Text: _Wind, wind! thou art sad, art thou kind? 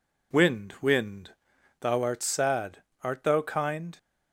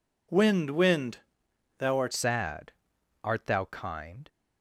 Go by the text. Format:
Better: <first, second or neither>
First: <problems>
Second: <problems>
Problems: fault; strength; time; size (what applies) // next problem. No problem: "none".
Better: first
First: none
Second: changes voice at "sad"; from 2.1 s on; 2.1 s long